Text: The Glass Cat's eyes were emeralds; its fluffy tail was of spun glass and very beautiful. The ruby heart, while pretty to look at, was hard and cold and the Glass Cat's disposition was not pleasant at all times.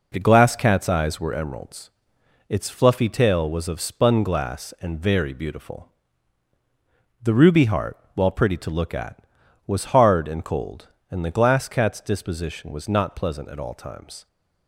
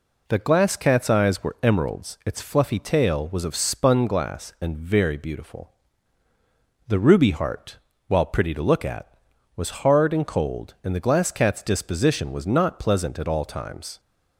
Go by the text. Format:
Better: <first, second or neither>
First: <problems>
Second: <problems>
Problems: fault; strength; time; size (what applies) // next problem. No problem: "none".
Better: neither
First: none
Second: none